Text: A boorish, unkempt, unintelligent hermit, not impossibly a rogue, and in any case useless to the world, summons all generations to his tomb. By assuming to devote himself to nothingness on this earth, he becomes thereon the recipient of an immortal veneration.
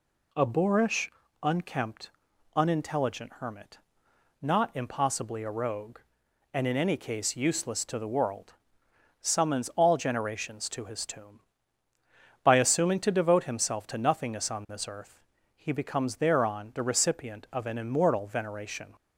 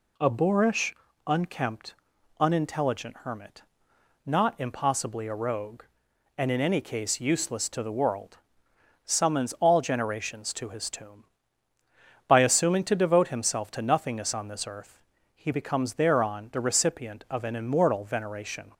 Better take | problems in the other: neither | none

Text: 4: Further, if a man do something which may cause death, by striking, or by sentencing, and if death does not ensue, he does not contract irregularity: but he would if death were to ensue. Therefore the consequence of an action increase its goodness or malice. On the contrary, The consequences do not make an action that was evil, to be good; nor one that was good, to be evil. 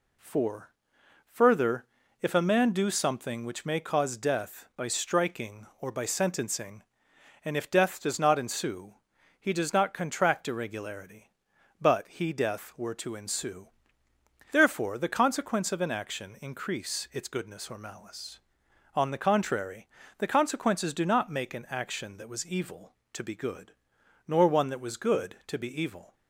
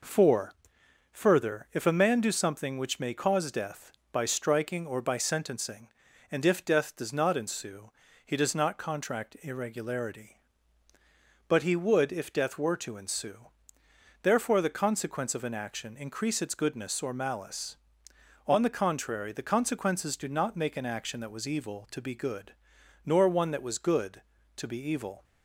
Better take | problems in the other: second | skips "would if"; at 12.3 s

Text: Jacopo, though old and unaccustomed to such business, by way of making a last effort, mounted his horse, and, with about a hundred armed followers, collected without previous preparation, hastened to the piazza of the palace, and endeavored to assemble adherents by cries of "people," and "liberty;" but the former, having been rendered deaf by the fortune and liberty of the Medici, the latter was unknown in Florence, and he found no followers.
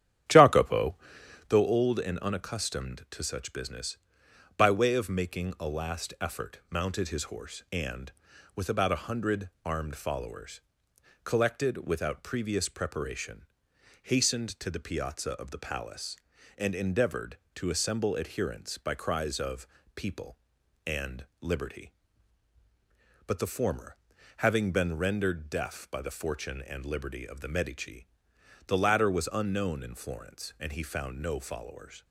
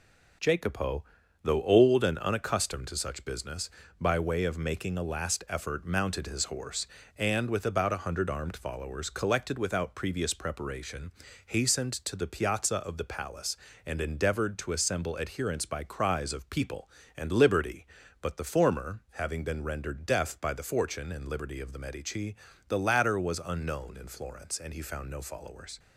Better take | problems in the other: second | starts louder than the rest; strong; until 1.5 s; 10.5 dB // pauses between "hundred" and "armed"; slight; at 9.4 s; 0.16 s long // pauses between "of" and "people"; slight; at 19.6 s; 0.28 s long

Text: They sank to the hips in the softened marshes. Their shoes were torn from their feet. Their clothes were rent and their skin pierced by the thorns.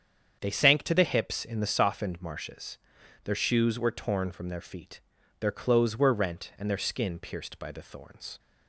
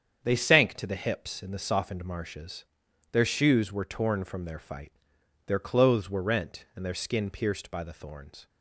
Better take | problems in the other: first | starts louder than the rest; strong; until 1.2 s; 8 dB; strong in the first // says "fight" for "feet"; at 4.5 s

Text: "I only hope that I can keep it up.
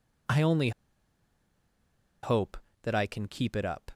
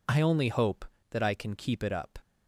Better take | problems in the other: second | pauses between "only" and "hope"; strong; at 0.7 s; 1.5 s long

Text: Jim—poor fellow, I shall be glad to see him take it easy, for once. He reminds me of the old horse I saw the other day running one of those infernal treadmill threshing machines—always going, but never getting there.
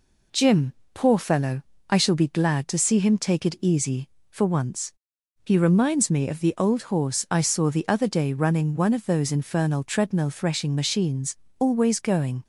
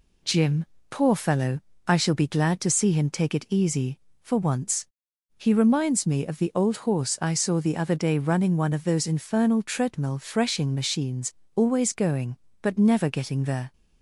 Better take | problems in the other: second | stops before "but never getting there"; at 12.4 s

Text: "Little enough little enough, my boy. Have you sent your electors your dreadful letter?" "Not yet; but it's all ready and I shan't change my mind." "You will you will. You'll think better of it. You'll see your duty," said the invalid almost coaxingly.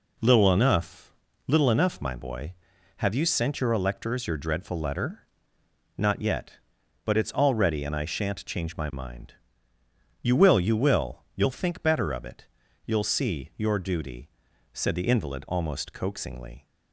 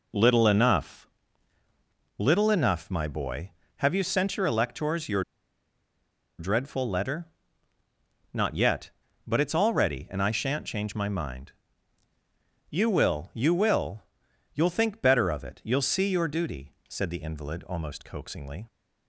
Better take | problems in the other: first | pauses between "enough" and "little"; at 1.0 s; 1.1 s long; slight in the first // pauses between "your" and "dreadful"; at 5.2 s; 1.1 s long

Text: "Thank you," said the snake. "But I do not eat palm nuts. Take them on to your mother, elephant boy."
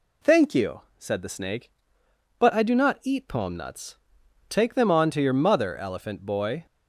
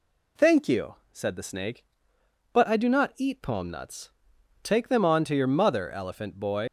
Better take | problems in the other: first | leaves "boy" unfinished; at 6.6 s; 115 ms

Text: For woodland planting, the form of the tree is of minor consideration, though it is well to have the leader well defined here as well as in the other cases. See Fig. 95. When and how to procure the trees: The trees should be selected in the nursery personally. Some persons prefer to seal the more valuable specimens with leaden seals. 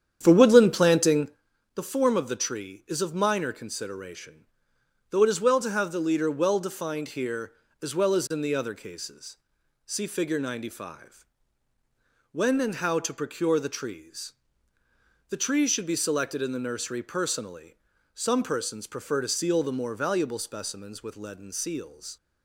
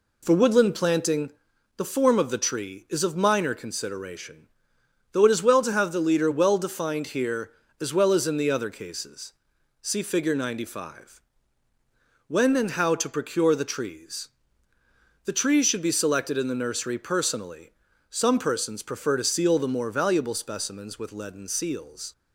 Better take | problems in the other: second | starts louder than the rest; strong; until 1.4 s; 9 dB

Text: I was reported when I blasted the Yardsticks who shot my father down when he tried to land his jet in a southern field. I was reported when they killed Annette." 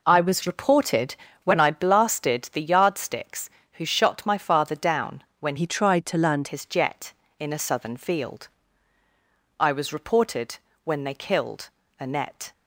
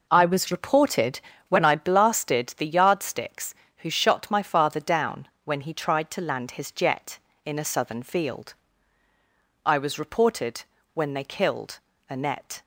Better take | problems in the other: second | pauses between "reported" and "when"; slight; at 1.1 s; 0.30 s long; slight in the second // pauses between "down" and "when"; slight; at 5.2 s; 0.16 s long; slight in the second // changes voice from "he" to "land"; from 5.5 to 6.4 s; 0.9 s long // pauses between "reported" and "when"; slight; at 10.5 s; 0.26 s long; slight in the second // pauses between "killed" and "Annette"; slight; at 11.6 s; 0.30 s long; slight in the second

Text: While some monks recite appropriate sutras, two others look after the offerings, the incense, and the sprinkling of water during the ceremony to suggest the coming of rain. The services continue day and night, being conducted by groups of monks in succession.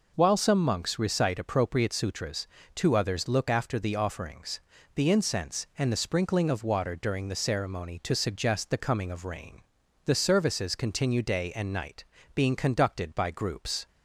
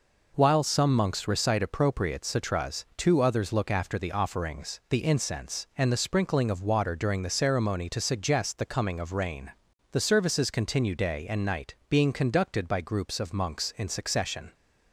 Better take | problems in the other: second | stops before "of monks in succession"; at 13.8 s

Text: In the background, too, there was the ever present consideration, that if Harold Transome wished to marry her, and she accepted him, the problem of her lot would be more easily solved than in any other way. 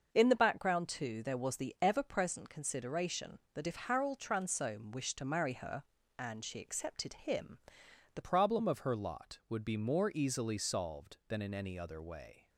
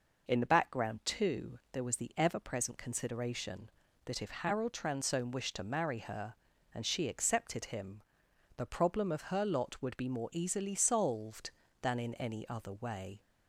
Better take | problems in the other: second | starts louder than the rest; until 1.1 s; 6 dB // changes voice at "problem"; from 8.2 s on; 4.2 s long

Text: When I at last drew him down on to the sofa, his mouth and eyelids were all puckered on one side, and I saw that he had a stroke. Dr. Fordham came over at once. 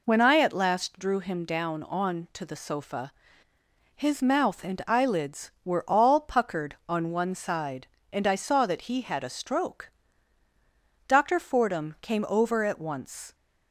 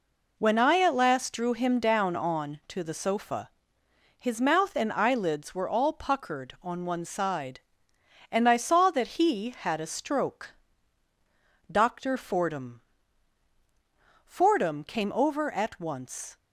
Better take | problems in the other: first | says "Fordham" twice; at 14.2 s

